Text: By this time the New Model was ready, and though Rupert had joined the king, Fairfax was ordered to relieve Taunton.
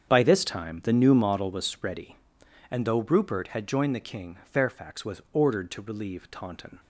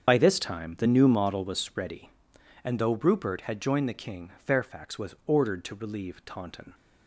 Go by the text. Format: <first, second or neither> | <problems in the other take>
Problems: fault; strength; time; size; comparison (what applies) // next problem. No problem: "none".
first | loses the start of "By"; at 0.0 s; 45 ms // starts louder than the rest; strong; until 1.1 s; 7.5 dB; strong in the first